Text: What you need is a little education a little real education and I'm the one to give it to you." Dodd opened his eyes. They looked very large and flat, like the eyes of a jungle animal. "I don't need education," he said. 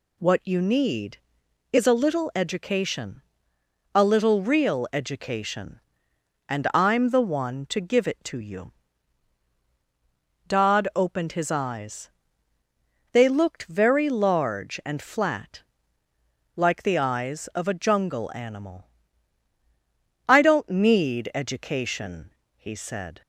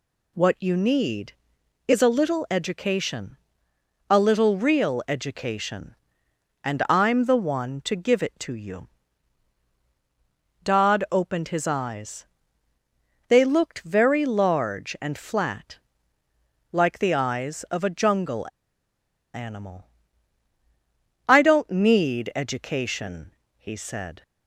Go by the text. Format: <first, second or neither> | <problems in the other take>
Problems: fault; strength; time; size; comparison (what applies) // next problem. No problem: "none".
first | pauses between "education" and "a"; noticeable; at 3.3 s; 0.74 s long; noticeable in the first // pauses between "jungle" and "animal"; noticeable; at 18.4 s; 0.87 s long